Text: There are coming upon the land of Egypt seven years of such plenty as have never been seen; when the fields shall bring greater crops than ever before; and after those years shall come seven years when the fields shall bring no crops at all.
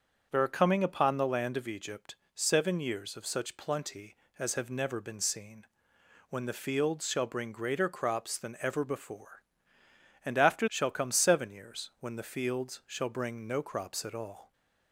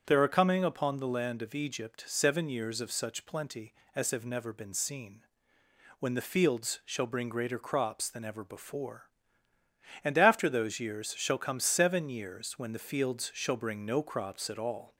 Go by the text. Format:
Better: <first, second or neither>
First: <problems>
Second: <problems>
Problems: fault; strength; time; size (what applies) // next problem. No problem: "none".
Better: second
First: starts louder than the rest; until 1.3 s; 7 dB // pauses between "Egypt" and "seven"; slight; at 2.1 s; 0.18 s long // skips "those years"; at 10.6 s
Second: starts louder than the rest; strong; until 1.0 s; 7.5 dB